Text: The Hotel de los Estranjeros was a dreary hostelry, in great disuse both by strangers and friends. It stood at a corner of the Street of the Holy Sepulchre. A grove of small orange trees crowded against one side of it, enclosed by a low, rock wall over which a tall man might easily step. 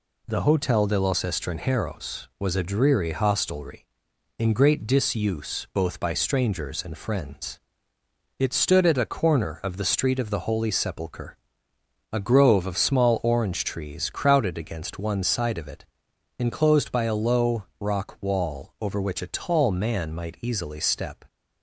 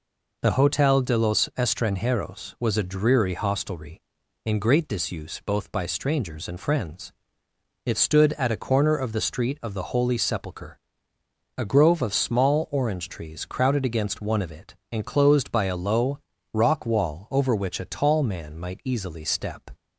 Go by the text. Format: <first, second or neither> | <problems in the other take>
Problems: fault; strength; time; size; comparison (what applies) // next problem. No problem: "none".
first | skips "side"; at 14.4 s